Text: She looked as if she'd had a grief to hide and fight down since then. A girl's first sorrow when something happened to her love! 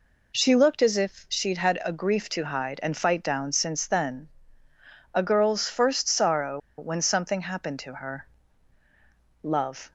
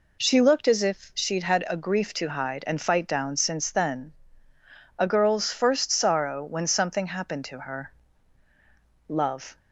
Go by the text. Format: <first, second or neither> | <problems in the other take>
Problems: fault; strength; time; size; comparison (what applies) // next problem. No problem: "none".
second | pauses between "sorrow" and "when"; slight; at 6.5 s; 0.19 s long // pauses between "her" and "love"; at 8.2 s; 1.1 s long; also in the second